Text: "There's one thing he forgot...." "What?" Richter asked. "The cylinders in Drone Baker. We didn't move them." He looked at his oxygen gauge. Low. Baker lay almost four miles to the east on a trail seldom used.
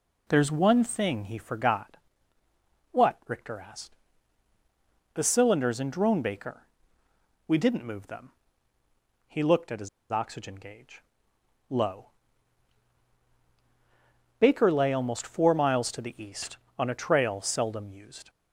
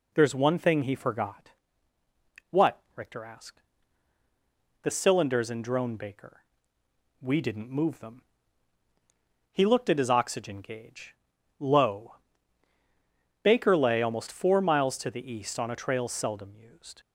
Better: second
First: pauses between "his" and "oxygen"; slight; at 9.8 s; 0.22 s long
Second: none

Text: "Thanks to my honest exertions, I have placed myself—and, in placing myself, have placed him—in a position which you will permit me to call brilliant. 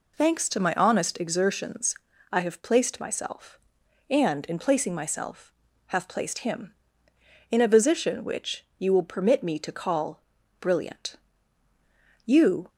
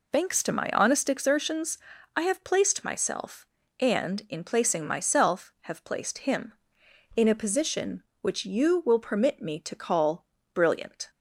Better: second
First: pauses between "call" and "brilliant"; at 10.2 s; 0.38 s long // goes on to say "You"; slight; from 12.2 s on; 0.44 s long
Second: pauses between "call" and "brilliant"; slight; at 10.2 s; 0.28 s long

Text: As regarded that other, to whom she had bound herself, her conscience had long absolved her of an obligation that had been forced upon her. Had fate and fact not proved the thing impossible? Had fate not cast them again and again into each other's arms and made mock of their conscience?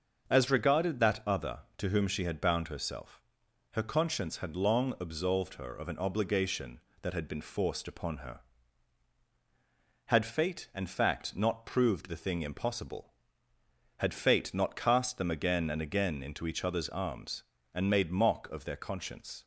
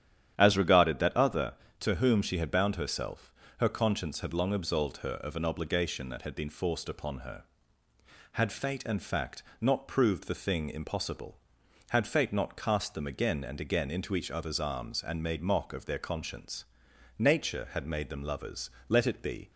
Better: first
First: starts louder than the rest; until 1.3 s; 6.5 dB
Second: starts louder than the rest; strong; until 1.3 s; 10.5 dB // pauses between "fact" and "not"; slight; at 9.4 s; 0.16 s long // goes on to say "Nature had made them lovers let it be"; strong; from 17.1 s on; 2.3 s long

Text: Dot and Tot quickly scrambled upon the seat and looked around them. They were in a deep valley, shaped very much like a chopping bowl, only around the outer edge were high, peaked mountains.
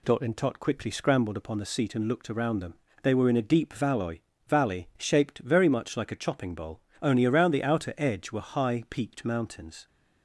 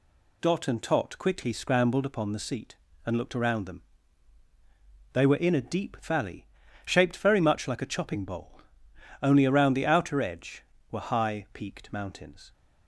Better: second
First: says "valley" twice; at 4.4 s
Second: none

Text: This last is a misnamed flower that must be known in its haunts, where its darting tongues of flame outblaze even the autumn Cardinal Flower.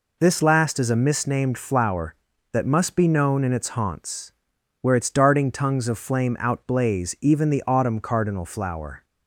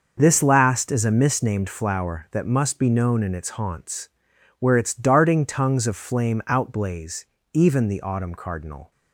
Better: first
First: none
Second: starts louder than the rest; until 1.1 s; 6 dB // pauses between "outblaze" and "even"; slight; at 7.2 s; 0.30 s long // stops before "Flower"; at 8.9 s

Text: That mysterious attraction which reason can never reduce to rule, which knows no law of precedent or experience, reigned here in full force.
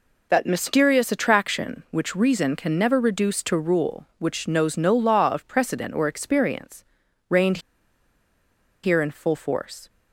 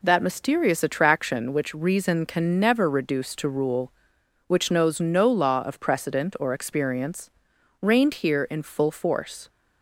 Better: second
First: pauses between "reigned" and "here"; strong; at 7.5 s; 1.2 s long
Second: none

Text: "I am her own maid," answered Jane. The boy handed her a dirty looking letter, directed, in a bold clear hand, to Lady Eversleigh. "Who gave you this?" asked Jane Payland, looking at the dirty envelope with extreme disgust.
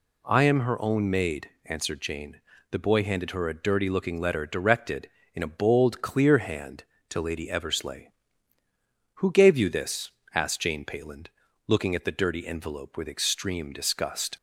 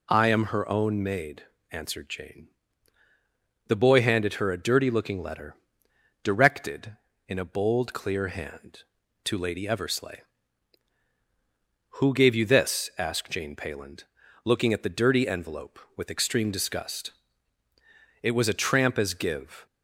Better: first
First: none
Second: goes on to say "It was a tramp as give"; from 18.2 s on; 1.4 s long

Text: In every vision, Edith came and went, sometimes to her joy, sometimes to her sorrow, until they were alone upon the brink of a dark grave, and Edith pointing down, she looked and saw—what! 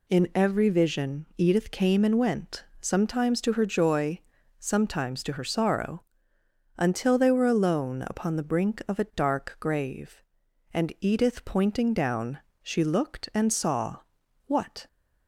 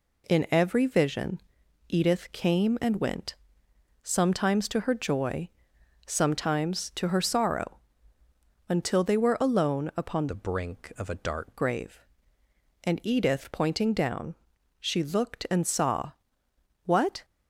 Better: first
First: none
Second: changes voice from "the" to "dark"; from 10.2 to 11.5 s; 1.3 s long

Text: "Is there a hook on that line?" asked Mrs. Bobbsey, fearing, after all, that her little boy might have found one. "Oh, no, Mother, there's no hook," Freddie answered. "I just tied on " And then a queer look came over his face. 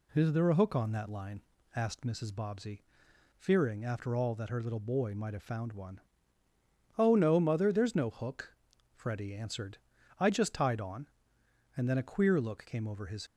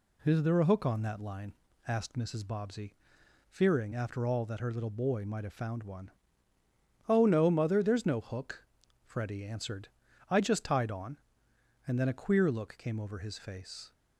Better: second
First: stops before "face"; at 13.2 s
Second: none

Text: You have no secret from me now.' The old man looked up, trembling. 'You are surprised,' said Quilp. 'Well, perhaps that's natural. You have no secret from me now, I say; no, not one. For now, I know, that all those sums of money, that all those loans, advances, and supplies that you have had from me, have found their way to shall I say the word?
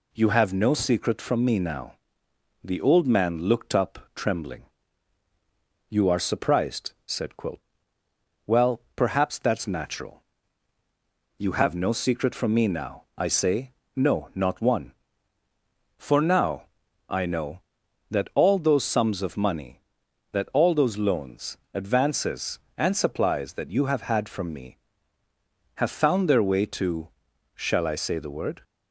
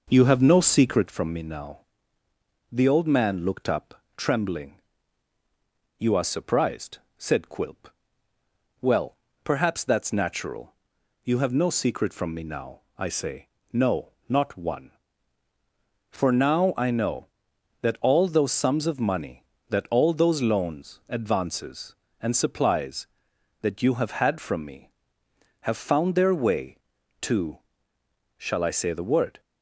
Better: first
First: pauses between "to" and "shall"; noticeable; at 27.0 s; 0.46 s long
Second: starts louder than the rest; noticeable; until 1.1 s; 5.5 dB // pauses between "to" and "shall"; noticeable; at 27.5 s; 0.80 s long

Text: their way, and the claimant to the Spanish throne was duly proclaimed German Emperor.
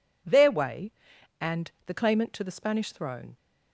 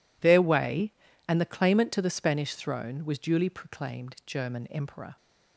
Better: second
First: pauses between "and" and "the"; slight; at 1.6 s; 0.16 s long // stops before "was duly proclaimed German Emperor"; at 3.3 s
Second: none

